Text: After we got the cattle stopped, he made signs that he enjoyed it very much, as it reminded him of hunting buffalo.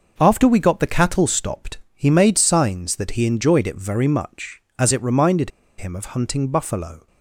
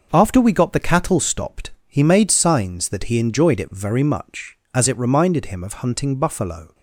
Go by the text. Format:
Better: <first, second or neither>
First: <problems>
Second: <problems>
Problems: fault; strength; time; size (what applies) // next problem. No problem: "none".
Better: second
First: starts louder than the rest; noticeable; until 1.1 s; 6 dB // pauses between "reminded" and "him"; slight; at 5.5 s; 0.28 s long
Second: starts louder than the rest; noticeable; until 1.1 s; 6 dB